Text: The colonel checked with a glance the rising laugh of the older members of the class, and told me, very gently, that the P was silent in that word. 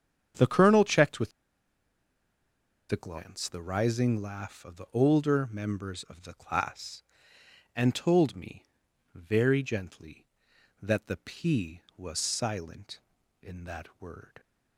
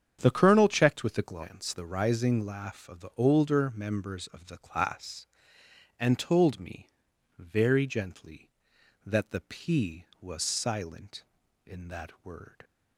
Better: second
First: starts louder than the rest; strong; until 2.9 s; 8 dB // pauses between "with" and "a"; strong; at 1.3 s; 1.6 s long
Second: starts louder than the rest; strong; until 1.2 s; 8 dB

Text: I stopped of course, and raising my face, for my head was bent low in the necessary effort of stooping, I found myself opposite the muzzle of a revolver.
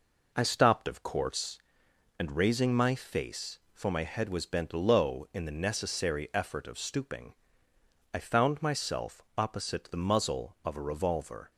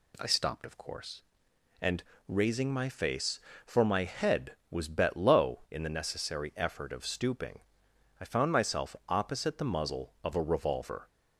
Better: first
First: none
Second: pauses between "and" and "raising"; slight; at 2.0 s; 0.26 s long // says "bet" for "bent"; at 4.8 s

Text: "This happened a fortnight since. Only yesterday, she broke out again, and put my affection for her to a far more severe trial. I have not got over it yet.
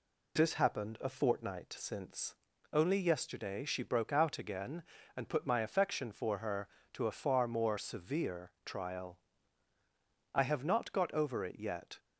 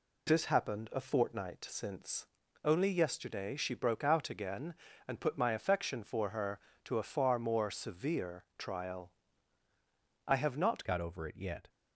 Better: first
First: none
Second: changes voice at "got"; from 10.8 s on; 0.8 s long

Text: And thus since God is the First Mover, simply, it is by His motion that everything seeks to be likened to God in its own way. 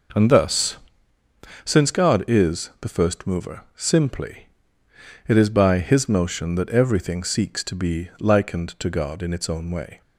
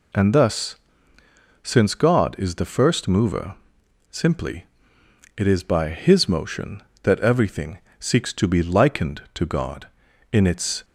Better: first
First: pauses between "thus" and "since"; noticeable; at 0.7 s; 0.86 s long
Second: pauses between "thus" and "since"; noticeable; at 0.7 s; 0.86 s long // pauses between "everything" and "seeks"; slight; at 7.7 s; 0.20 s long // stops before "own way"; at 10.8 s

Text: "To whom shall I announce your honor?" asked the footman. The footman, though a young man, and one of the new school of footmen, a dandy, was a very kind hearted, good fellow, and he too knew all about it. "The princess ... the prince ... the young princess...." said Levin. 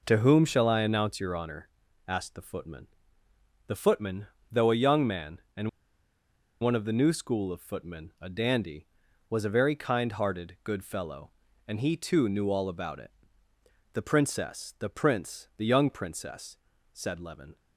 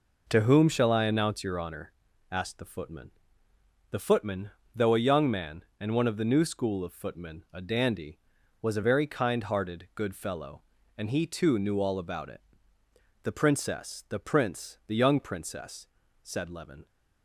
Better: second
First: pauses between "and" and "one"; noticeable; at 5.6 s; 0.93 s long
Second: none

